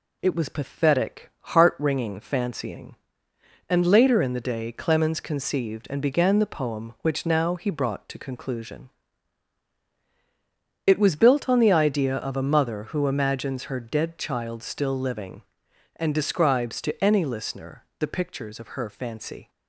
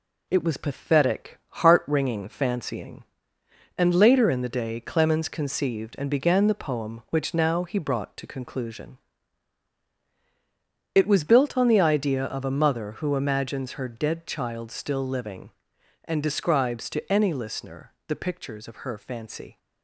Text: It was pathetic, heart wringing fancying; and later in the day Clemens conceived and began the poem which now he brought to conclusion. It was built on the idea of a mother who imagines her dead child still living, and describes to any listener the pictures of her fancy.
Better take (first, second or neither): first